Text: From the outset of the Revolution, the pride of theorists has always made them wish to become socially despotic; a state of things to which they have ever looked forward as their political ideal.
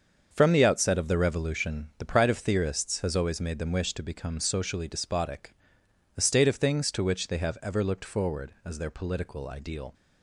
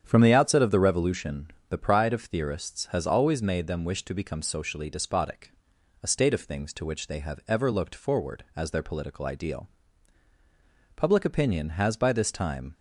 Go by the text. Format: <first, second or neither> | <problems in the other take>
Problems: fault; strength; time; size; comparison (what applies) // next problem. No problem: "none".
first | starts louder than the rest; strong; until 1.0 s; 8.5 dB; also in the first // goes on to say "Public opinion has by this time"; strong; from 10.9 s on; 1.7 s long